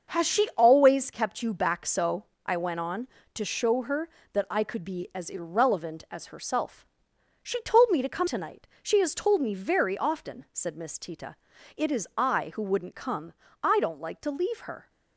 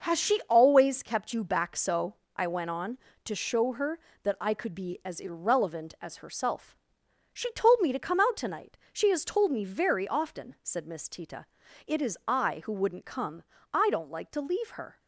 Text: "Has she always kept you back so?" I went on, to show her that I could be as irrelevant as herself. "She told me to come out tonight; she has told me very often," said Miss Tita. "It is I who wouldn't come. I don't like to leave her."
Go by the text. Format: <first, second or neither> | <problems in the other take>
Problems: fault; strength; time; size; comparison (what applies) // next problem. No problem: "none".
second | starts louder than the rest; until 1.2 s; 6.5 dB; noticeable in the second // skips "out"; at 8.2 s